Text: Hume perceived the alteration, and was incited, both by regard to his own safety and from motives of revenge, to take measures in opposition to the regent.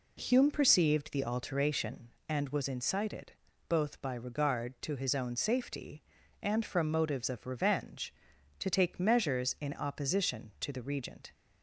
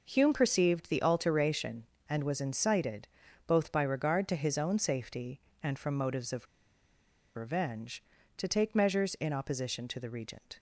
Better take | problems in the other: first | pauses between "of" and "revenge"; noticeable; at 6.4 s; 0.90 s long

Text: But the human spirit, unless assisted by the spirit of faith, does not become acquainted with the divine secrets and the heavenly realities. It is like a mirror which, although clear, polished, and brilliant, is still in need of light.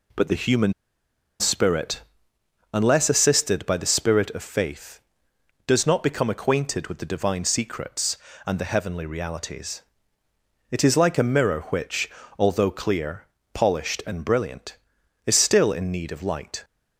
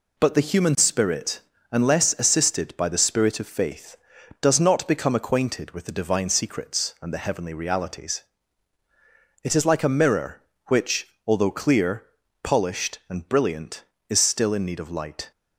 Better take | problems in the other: second | pauses between "human" and "spirit"; noticeable; at 0.7 s; 0.67 s long

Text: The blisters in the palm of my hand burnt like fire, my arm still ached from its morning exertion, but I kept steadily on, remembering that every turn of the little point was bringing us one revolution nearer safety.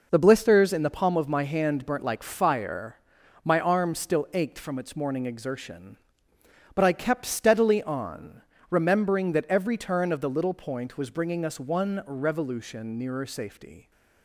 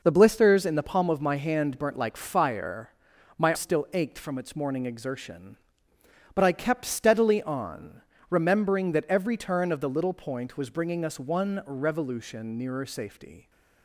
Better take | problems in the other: first | skips "arm"; at 3.5 s

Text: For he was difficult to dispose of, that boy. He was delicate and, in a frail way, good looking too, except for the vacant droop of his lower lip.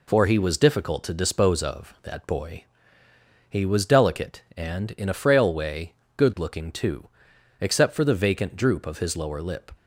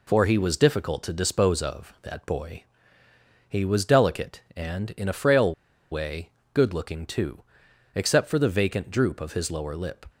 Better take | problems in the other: first | pauses between "frail" and "way"; at 5.5 s; 0.39 s long

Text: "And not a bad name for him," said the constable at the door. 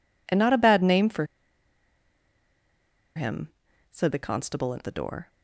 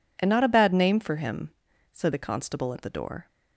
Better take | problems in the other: second | pauses between "for" and "him"; strong; at 1.2 s; 1.9 s long

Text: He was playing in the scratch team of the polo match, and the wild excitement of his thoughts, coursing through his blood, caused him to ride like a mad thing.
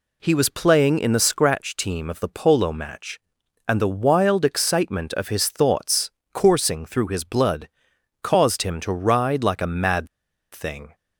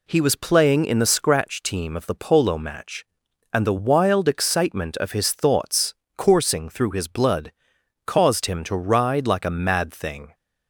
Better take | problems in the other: second | pauses between "mad" and "thing"; at 10.0 s; 0.45 s long

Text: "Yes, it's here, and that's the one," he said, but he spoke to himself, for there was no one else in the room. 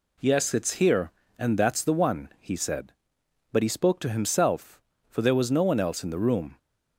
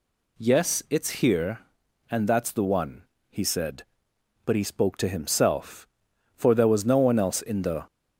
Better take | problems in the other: first | stops before "room"; at 7.8 s

